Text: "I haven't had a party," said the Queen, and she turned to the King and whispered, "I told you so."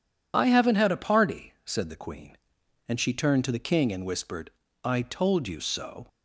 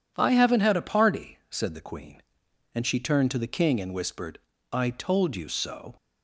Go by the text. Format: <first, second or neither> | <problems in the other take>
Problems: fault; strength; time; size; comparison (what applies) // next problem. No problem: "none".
second | loses the start of "I"; at 0.3 s; 35 ms